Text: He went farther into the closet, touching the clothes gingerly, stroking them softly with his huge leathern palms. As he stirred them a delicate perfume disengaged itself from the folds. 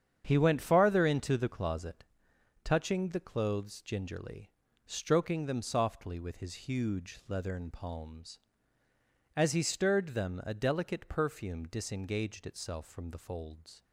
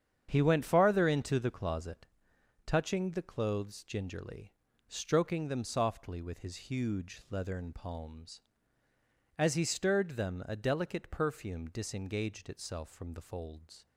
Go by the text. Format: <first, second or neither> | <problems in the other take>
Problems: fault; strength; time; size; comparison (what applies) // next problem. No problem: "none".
neither | starts louder than the rest; strong; the same in both